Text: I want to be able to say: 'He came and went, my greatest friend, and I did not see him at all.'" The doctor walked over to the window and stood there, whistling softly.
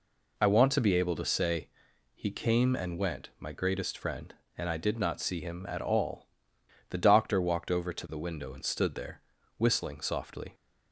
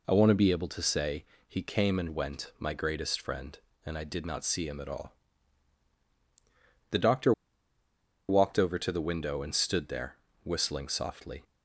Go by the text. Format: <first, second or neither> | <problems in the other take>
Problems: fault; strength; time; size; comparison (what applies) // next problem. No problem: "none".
first | pauses between "doctor" and "walked"; noticeable; at 7.3 s; 0.96 s long